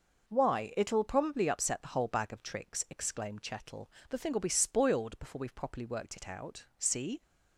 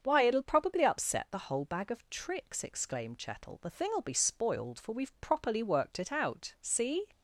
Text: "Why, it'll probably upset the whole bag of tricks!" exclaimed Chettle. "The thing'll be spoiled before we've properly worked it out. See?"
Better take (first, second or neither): first